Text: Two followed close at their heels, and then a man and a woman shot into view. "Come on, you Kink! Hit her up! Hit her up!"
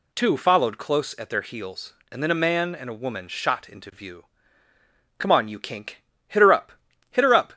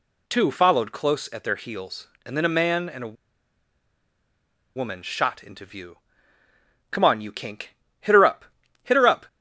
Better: first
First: none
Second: pauses between "a" and "woman"; strong; at 3.1 s; 1.6 s long

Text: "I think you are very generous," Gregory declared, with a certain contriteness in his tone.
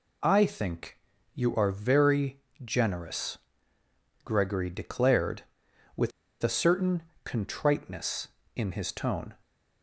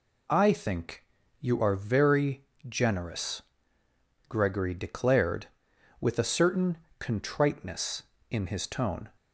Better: second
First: pauses between "think" and "you"; slight; at 0.9 s; 0.34 s long // pauses between "very" and "generous"; slight; at 2.4 s; 0.22 s long // pauses between "with" and "a"; slight; at 6.1 s; 0.30 s long // pauses between "certain" and "contriteness"; slight; at 7.0 s; 0.20 s long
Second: pauses between "think" and "you"; slight; at 1.0 s; 0.34 s long // pauses between "very" and "generous"; slight; at 2.4 s; 0.22 s long // pauses between "certain" and "contriteness"; slight; at 6.7 s; 0.20 s long

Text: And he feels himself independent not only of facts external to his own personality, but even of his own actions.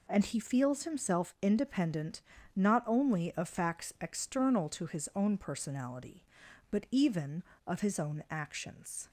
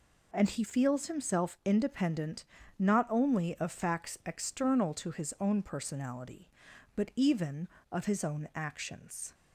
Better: neither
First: pauses between "independent" and "not"; slight; at 2.2 s; 0.34 s long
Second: pauses between "independent" and "not"; slight; at 2.4 s; 0.34 s long

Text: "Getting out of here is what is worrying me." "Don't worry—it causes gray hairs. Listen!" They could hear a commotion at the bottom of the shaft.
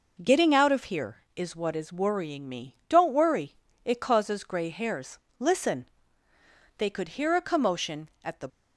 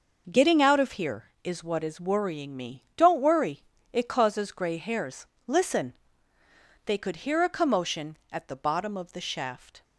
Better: second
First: stops before "bottom of the shaft"; at 8.4 s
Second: none

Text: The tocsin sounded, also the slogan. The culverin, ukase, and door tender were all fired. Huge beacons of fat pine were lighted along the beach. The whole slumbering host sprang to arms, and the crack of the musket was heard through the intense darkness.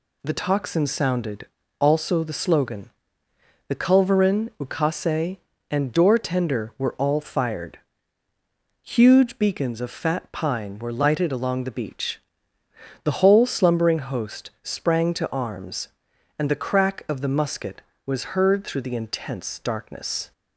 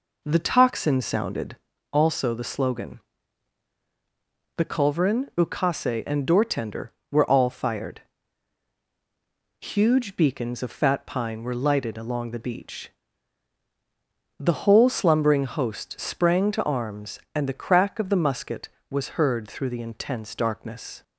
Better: first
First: none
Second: starts louder than the rest; noticeable; until 1.8 s; 4 dB

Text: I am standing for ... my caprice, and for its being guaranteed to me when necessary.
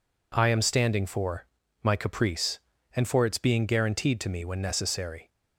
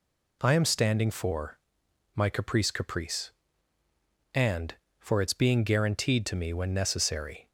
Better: first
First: none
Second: says "caprice" twice; at 2.7 s

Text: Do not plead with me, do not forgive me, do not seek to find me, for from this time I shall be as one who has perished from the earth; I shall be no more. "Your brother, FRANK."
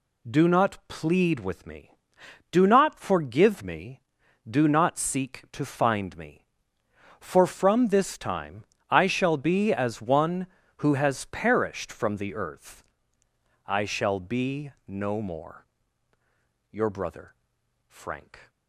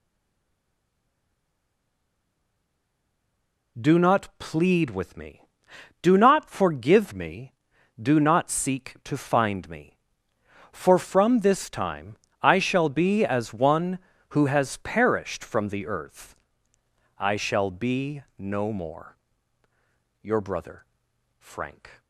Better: first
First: pauses between "time" and "I"; slight; at 8.6 s; 0.24 s long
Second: stays silent before the first word; strong; until 3.7 s; 3.7 s long // pauses between "time" and "I"; slight; at 12.1 s; 0.24 s long

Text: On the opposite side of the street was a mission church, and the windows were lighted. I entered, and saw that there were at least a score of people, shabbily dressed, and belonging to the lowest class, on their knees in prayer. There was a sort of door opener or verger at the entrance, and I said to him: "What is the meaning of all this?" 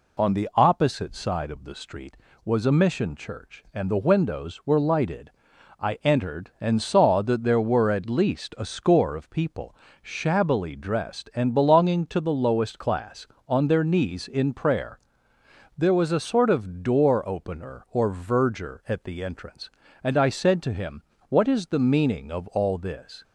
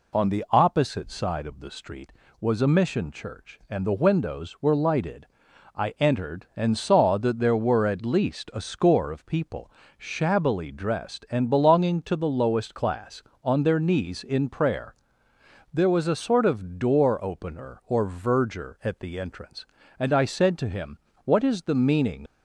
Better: first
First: none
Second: stops before "of all this"; at 22.2 s

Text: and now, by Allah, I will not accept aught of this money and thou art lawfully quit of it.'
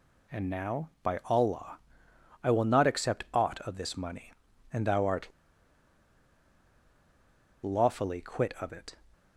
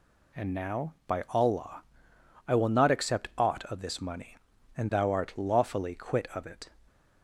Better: second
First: pauses between "art" and "lawfully"; strong; at 5.2 s; 2.3 s long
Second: none

